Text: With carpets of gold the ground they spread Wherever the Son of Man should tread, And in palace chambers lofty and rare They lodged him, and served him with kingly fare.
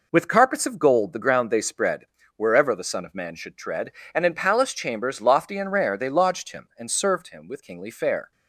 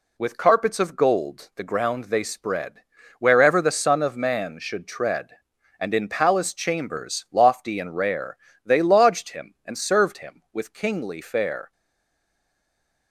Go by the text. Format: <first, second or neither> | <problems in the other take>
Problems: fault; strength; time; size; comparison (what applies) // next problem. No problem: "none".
first | pauses between "spread" and "Wherever"; slight; at 2.8 s; 0.36 s long; slight in the first // pauses between "rare" and "They"; slight; at 8.3 s; 0.26 s long // stays silent after the last word; noticeable; from 11.7 s on; 1.4 s long